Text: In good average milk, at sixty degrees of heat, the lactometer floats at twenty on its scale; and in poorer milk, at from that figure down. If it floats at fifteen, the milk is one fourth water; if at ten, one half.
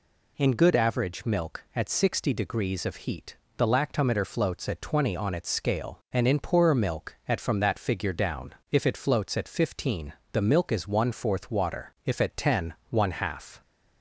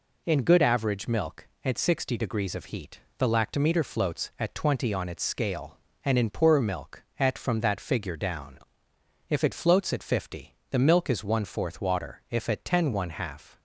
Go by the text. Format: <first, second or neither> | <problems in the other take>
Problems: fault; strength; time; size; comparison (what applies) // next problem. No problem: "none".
first | says "fifty" for "fifteen"; at 10.0 s